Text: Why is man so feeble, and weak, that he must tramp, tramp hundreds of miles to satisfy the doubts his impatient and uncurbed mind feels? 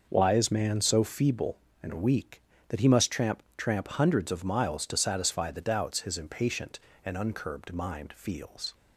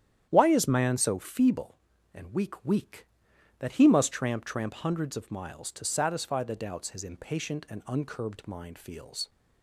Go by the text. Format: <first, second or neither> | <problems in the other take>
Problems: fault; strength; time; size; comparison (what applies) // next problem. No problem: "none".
first | starts louder than the rest; strong; until 1.3 s; 10 dB; also in the first // says "weak" twice; at 2.6 s